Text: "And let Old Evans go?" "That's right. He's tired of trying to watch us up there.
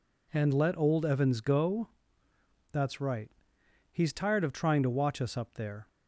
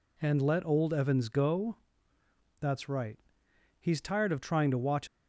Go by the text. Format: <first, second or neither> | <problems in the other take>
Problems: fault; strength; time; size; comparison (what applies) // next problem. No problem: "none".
first | stops before "us up there"; at 5.0 s